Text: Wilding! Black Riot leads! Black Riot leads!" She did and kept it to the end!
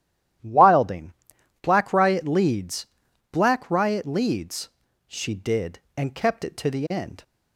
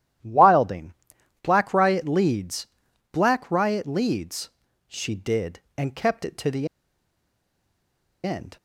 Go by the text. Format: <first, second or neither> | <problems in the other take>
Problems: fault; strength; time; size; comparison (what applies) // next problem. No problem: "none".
first | starts louder than the rest; strong; until 1.7 s; 12 dB; strong in the first // pauses between "the" and "end"; strong; at 6.6 s; 1.5 s long